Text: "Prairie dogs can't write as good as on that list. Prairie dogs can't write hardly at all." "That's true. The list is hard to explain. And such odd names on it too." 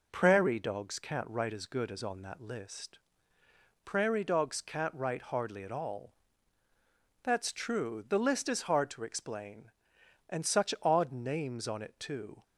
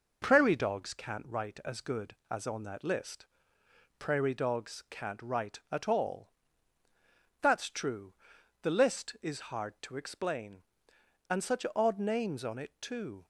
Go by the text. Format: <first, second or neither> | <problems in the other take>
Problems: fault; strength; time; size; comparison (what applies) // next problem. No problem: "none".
first | skips "hardly"; at 5.6 s